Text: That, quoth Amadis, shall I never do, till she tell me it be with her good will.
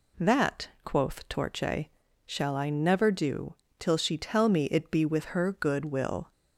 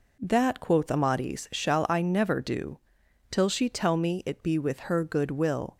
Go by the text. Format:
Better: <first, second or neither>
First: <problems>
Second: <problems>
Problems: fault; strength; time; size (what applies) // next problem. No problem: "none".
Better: second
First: says "Torche" for "Amadis"; at 1.2 s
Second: none